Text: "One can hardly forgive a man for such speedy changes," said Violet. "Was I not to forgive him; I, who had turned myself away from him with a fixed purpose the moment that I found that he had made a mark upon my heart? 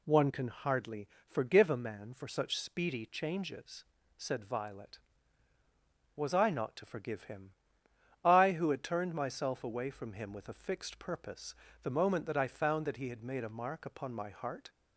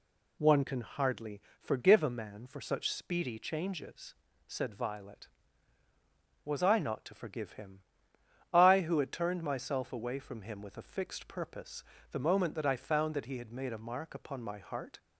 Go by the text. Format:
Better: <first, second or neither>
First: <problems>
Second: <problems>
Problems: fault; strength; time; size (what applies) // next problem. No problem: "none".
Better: neither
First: pauses between "hardly" and "forgive"; slight; at 1.0 s; 0.18 s long // pauses between "purpose" and "the"; slight; at 11.5 s; 0.26 s long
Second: pauses between "hardly" and "forgive"; slight; at 1.4 s; 0.18 s long // pauses between "purpose" and "the"; slight; at 11.8 s; 0.26 s long